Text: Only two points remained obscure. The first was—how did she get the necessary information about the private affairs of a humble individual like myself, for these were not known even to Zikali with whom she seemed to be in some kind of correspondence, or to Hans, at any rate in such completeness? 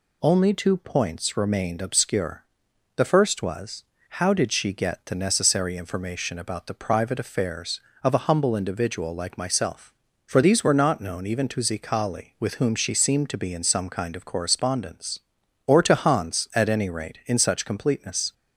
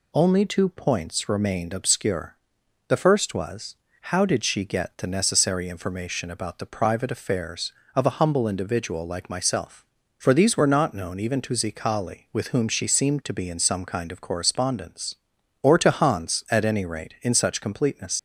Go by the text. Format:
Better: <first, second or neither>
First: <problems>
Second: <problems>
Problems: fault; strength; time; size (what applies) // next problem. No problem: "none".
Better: first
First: none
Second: leaves "completeness" unfinished; at 18.1 s; 95 ms